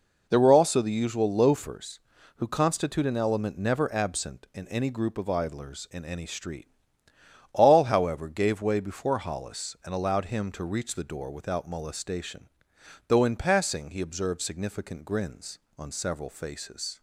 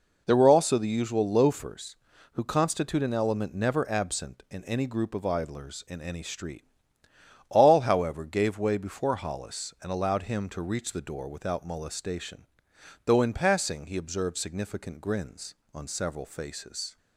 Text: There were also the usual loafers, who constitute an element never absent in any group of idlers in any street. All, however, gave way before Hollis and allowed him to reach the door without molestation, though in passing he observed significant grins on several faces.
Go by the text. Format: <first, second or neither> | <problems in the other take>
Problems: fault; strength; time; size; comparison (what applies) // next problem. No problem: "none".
neither | none